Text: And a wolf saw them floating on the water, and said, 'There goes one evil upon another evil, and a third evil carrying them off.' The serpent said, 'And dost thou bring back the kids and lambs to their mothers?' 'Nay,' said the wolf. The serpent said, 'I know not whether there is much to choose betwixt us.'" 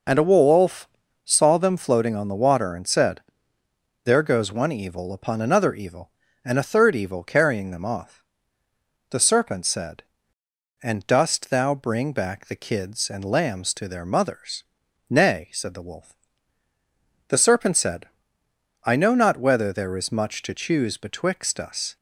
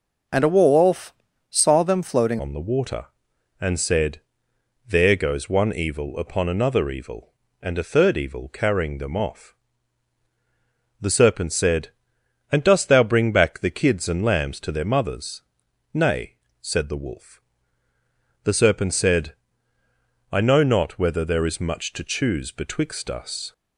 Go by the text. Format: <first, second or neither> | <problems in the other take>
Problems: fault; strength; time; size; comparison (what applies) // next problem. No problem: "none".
first | pauses between "wolf" and "saw"; at 1.1 s; 0.38 s long; also in the first // changes voice at "on"; from 2.3 s on; 21.2 s long